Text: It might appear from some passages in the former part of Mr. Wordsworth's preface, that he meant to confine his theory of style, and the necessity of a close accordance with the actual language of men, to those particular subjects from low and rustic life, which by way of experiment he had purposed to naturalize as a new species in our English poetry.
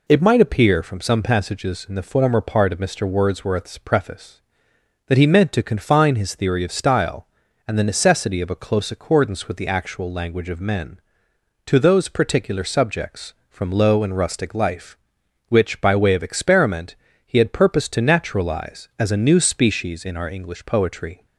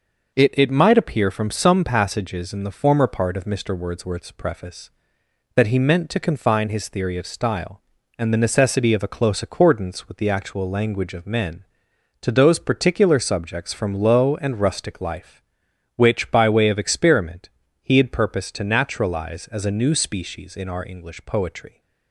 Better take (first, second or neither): first